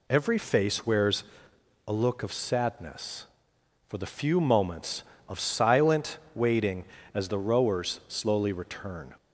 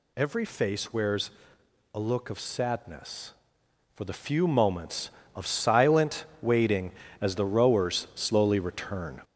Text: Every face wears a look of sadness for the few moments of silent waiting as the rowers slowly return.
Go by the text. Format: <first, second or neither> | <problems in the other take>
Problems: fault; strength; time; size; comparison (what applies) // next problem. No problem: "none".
first | gets louder; noticeable; throughout; 5 dB // pauses between "wears" and "a"; noticeable; at 1.2 s; 0.64 s long; noticeable in the first // pauses between "silent" and "waiting"; slight; at 6.2 s; 0.16 s long; slight in the first